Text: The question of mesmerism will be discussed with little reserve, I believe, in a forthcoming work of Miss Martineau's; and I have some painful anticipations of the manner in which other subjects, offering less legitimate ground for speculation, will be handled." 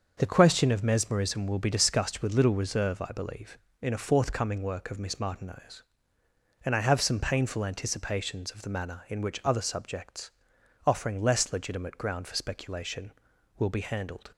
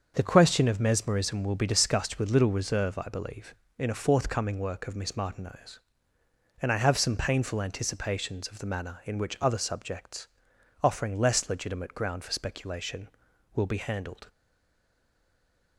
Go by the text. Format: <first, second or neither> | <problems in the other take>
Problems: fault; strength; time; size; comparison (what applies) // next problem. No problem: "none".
first | starts louder than the rest; until 1.1 s; 6.5 dB; also in the first // stays silent after the last word; noticeable; from 14.2 s on; 1.5 s long